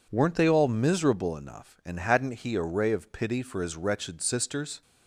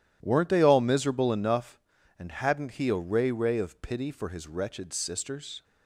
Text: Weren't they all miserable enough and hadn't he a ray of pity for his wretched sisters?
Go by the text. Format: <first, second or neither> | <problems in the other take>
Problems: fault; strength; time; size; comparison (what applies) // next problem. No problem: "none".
first | says "ray" twice; at 3.3 s